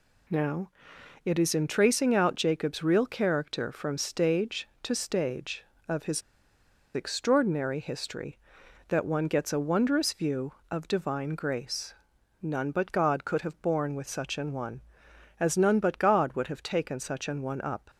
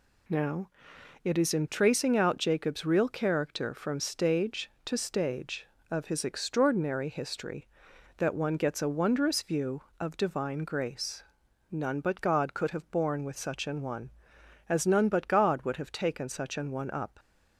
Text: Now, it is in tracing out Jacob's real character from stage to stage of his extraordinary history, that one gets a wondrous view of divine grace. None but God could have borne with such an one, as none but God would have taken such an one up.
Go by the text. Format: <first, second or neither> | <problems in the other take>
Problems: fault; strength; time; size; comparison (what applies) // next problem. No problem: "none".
second | pauses between "his" and "extraordinary"; noticeable; at 6.2 s; 0.74 s long